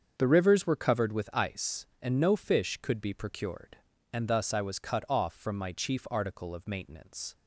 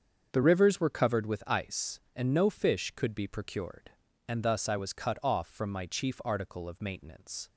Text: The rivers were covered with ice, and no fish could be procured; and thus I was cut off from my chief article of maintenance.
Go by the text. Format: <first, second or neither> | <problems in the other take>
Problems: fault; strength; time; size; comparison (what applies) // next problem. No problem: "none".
neither | starts louder than the rest; the same in both